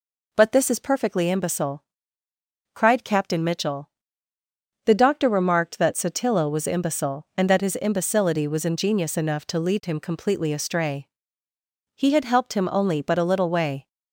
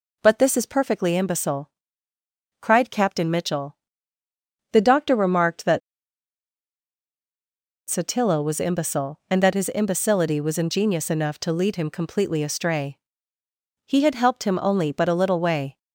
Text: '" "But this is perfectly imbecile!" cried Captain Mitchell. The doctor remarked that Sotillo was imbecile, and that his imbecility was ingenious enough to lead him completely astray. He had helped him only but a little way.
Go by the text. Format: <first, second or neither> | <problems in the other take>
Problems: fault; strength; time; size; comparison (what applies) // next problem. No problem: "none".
first | pauses between "that" and "Sotillo"; strong; at 5.8 s; 2.0 s long